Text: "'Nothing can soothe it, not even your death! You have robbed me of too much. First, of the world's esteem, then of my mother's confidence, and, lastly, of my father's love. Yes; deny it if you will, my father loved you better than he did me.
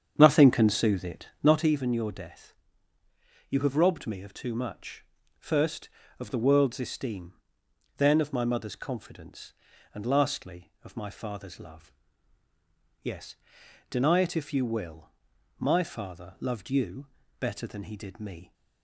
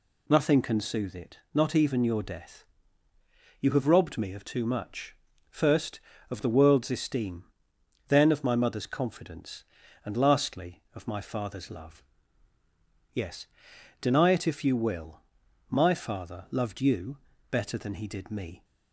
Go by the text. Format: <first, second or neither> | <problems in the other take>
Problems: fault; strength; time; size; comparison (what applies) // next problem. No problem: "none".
second | starts louder than the rest; strong; until 1.7 s; 8 dB // pauses between "you" and "better"; slight; at 17.0 s; 0.32 s long; slight in the second